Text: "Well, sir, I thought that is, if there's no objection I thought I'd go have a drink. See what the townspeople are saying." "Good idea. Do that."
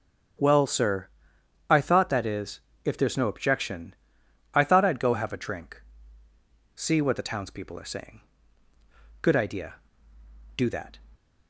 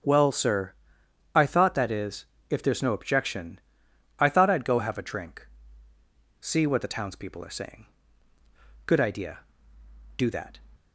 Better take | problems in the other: neither | starts louder than the rest; strong; the same in both // pauses between "objection" and "I"; noticeable; the same in both

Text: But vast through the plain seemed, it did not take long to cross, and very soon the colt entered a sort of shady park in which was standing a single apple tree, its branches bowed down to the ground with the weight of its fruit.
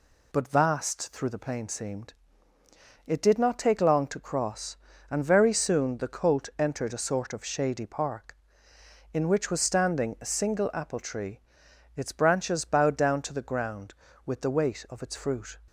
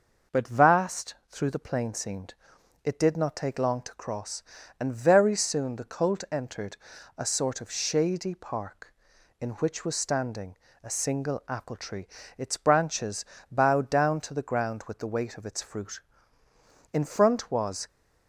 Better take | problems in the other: first | pauses between "vast" and "through"; slight; at 1.1 s; 0.16 s long // pauses between "entered" and "a"; at 6.7 s; 0.40 s long // pauses between "standing" and "a"; slight; at 10.5 s; 0.28 s long // pauses between "branches" and "bowed"; slight; at 13.2 s; 0.26 s long // goes on to say "In front was"; noticeable; from 16.9 s on; 0.94 s long

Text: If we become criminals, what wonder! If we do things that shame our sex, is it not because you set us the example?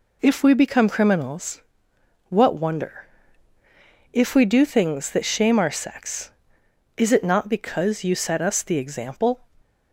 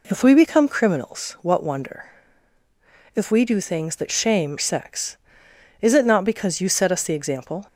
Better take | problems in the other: first | skips "our"; at 4.5 s

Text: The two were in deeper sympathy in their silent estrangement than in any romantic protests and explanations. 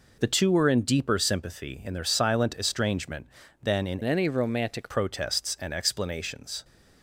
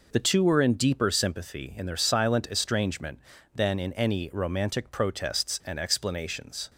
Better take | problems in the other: second | changes voice from "any" to "romantic"; from 4.0 to 4.9 s; 0.9 s long

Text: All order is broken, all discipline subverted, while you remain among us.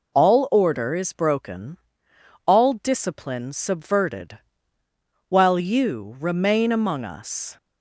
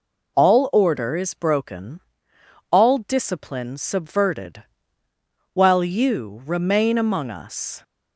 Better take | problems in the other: neither | none

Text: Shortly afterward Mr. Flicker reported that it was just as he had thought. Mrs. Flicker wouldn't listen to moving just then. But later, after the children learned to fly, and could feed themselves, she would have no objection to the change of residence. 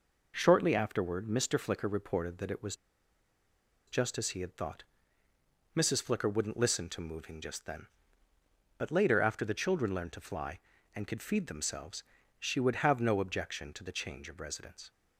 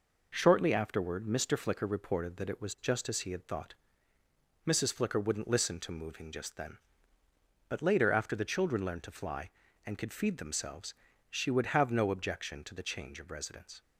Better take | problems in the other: second | pauses between "was" and "just"; at 2.7 s; 1.1 s long

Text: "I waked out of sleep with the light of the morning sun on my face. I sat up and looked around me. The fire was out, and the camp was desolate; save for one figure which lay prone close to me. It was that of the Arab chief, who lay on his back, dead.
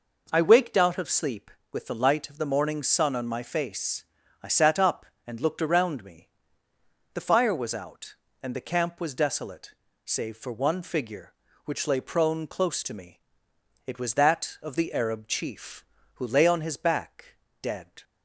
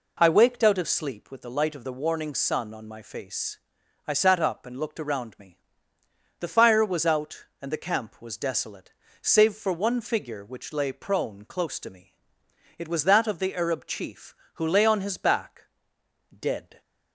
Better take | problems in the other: first | says "warning" for "morning"; at 1.9 s

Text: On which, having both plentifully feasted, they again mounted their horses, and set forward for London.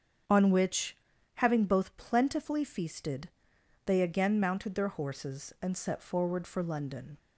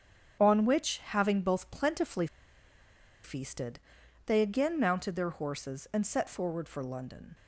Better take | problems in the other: first | starts louder than the rest; strong; until 1.4 s; 8 dB; strong in the first // pauses between "plentifully" and "feasted"; noticeable; at 2.2 s; 0.98 s long

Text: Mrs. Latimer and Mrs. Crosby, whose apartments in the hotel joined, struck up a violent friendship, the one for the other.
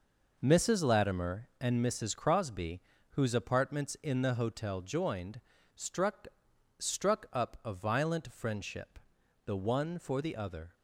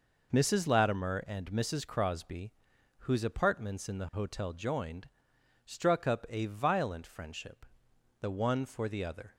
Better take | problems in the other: second | says "struck" twice; at 6.7 s

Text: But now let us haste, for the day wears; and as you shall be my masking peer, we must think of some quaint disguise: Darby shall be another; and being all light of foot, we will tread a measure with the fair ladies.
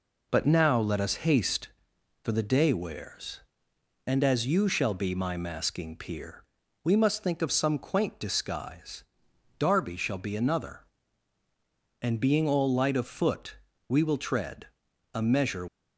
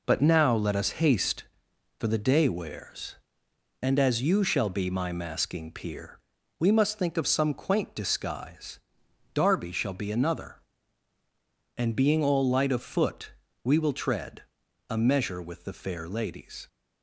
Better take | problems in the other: second | pauses between "tread" and "a"; noticeable; at 14.6 s; 0.46 s long; noticeable in the second // stops before "with the fair ladies"; at 15.6 s

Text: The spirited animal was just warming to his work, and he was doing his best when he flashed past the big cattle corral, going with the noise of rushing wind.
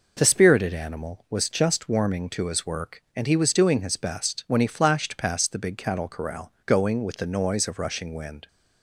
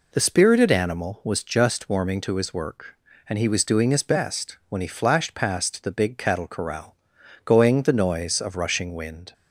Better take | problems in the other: first | skips "with"; at 7.8 s

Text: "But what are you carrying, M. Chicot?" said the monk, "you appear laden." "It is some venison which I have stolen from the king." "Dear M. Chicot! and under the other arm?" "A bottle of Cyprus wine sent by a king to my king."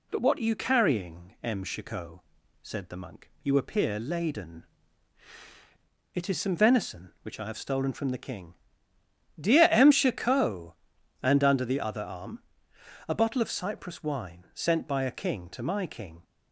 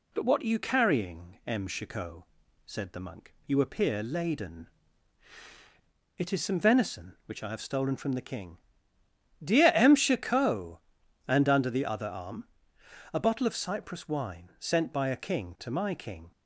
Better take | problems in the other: neither | none

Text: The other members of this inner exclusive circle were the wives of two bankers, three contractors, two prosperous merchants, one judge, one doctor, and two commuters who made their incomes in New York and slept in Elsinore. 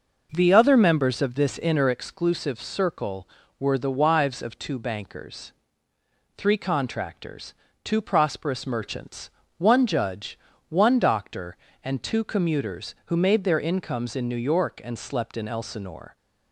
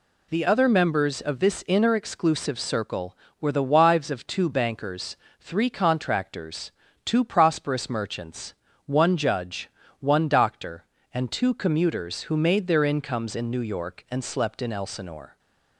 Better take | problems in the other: second | starts louder than the rest; noticeable; until 1.9 s; 5.5 dB

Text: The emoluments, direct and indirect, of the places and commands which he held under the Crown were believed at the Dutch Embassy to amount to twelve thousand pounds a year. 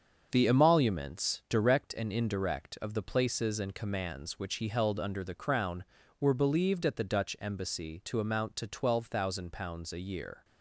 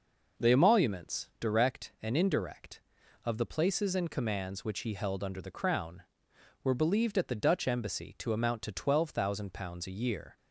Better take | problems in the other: second | gets quieter; throughout; 6.5 dB

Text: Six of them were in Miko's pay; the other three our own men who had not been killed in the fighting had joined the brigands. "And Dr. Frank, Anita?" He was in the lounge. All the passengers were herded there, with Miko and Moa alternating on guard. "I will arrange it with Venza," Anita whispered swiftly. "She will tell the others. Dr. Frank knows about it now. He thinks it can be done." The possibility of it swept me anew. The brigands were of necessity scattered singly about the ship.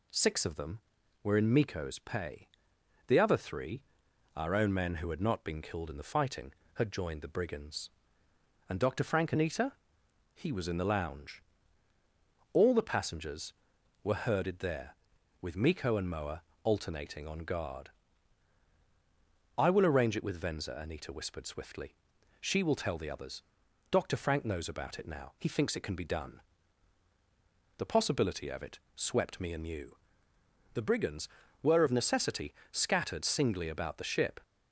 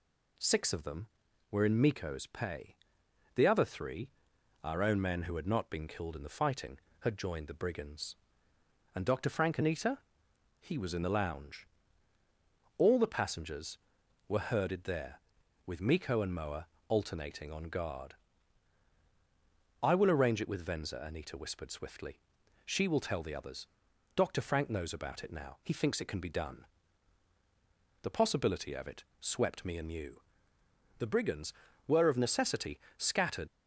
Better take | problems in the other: first | pauses between "three" and "our"; noticeable; at 4.1 s; 0.52 s long; noticeable in the first // pauses between "Moa" and "alternating"; slight; at 16.6 s; 0.20 s long; slight in the first // pauses between "it" and "swept"; slight; at 29.0 s; 0.16 s long; slight in the first // pauses between "necessity" and "scattered"; slight; at 32.7 s; 0.20 s long; slight in the first // stops before "singly about the ship"; at 33.4 s

